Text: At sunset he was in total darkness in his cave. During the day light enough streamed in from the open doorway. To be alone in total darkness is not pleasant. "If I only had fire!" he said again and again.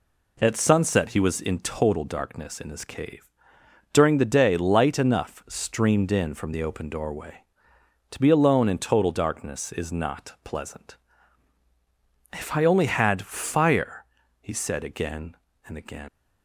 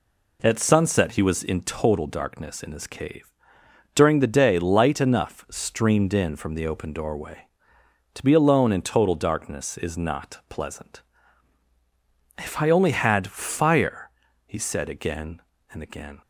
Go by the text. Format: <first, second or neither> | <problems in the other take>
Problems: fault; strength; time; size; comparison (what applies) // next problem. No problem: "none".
second | leaves "again" unfinished; at 16.0 s; 85 ms